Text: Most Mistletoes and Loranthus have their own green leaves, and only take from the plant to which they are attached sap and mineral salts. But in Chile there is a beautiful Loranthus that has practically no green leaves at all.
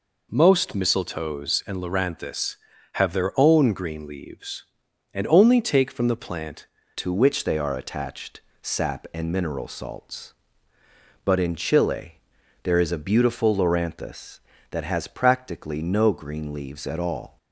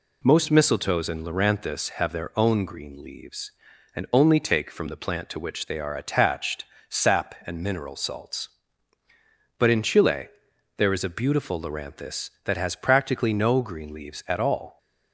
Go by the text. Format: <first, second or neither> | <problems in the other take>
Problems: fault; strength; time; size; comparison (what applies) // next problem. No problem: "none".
second | changes voice at "to"; from 6.9 s on; 10.4 s long // pauses between "attached" and "sap"; slight; at 8.4 s; 0.20 s long; slight in the second // pauses between "Chile" and "there"; noticeable; at 12.1 s; 0.46 s long; noticeable in the second